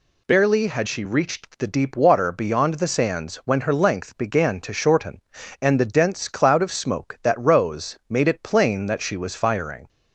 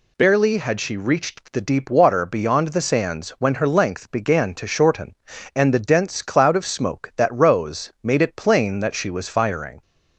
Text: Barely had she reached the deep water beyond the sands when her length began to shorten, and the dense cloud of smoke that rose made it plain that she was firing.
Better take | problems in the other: neither | none

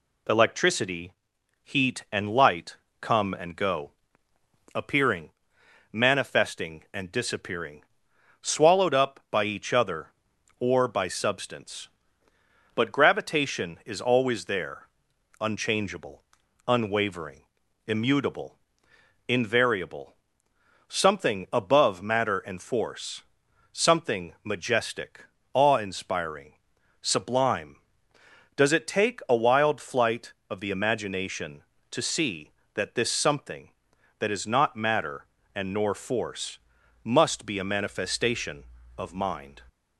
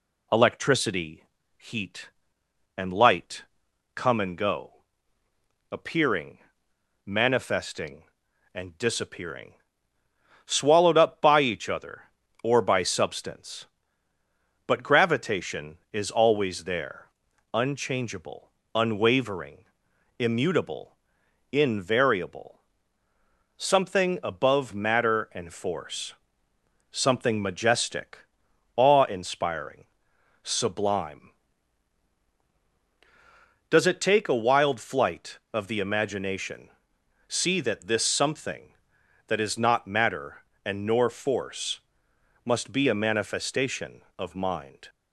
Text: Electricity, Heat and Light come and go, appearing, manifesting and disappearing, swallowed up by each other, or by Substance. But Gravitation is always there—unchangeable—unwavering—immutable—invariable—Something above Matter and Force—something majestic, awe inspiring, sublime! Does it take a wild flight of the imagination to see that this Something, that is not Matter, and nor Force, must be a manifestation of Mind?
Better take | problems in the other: first | pauses between "Light" and "come"; noticeable; at 3.4 s; 0.50 s long; slight in the first // skips "to"; at 36.9 s

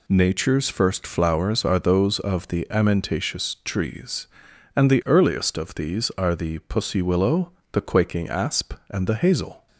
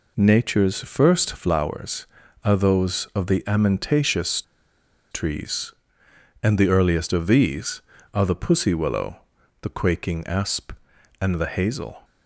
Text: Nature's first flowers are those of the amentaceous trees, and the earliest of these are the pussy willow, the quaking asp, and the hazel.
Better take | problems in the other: first | pauses between "amentaceous" and "trees"; noticeable; at 4.4 s; 0.70 s long

